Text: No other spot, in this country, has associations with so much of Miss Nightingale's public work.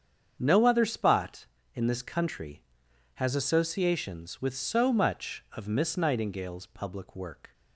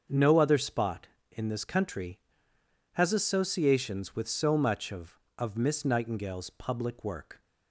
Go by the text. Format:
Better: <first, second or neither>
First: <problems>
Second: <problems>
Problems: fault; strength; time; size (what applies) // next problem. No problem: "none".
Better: first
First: starts louder than the rest; strong; until 1.3 s; 7.5 dB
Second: starts louder than the rest; until 1.3 s; 7 dB // says "of" twice; at 5.3 s